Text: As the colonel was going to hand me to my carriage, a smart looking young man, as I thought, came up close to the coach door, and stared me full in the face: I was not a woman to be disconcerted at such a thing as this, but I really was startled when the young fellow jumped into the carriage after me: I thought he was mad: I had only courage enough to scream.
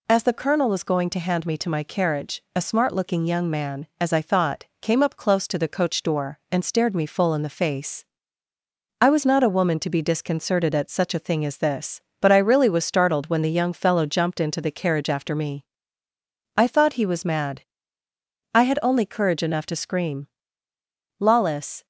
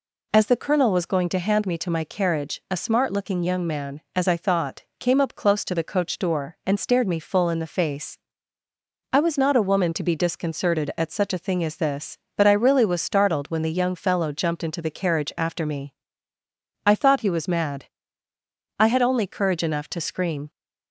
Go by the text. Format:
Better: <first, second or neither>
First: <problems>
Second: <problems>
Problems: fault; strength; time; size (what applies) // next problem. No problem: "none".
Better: second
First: goes on to say "Lawless"; noticeable; from 21.1 s on; 0.68 s long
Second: none